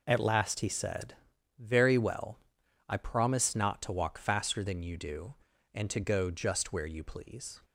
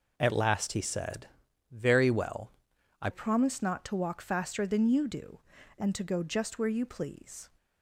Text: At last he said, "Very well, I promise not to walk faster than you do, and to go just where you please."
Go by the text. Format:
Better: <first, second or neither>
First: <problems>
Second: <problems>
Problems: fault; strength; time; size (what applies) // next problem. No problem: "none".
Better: first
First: none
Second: changes voice at "promise"; from 3.1 s on; 4.3 s long